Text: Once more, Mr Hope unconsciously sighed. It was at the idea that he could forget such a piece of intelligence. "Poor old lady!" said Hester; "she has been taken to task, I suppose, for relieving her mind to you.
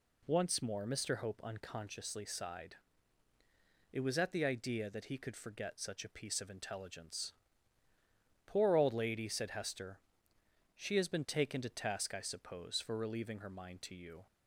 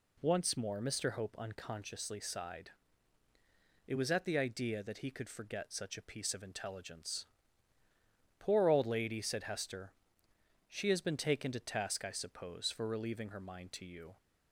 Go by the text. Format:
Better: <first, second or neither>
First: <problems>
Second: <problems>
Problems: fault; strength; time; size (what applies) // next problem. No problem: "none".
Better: neither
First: none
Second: none